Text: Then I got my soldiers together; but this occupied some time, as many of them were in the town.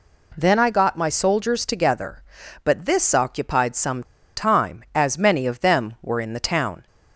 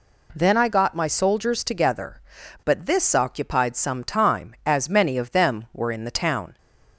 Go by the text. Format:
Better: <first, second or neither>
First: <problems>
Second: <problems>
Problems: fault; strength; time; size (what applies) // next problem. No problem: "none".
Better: second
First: pauses between "some" and "time"; slight; at 4.0 s; 0.32 s long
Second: none